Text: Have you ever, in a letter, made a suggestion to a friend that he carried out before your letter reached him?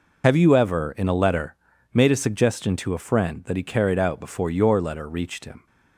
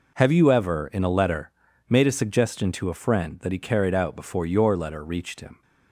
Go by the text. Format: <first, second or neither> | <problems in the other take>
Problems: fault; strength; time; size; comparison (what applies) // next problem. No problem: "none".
second | loses the start of "Have"; at 0.2 s; 45 ms